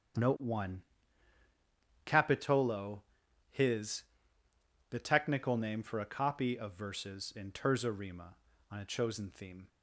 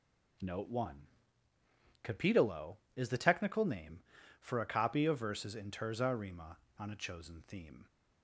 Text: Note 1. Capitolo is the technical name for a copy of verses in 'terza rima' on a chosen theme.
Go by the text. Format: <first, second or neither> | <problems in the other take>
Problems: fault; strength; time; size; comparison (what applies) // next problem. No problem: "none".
second | starts louder than the rest; strong; until 2.4 s; 7.5 dB // says "his" for "is"; at 3.5 s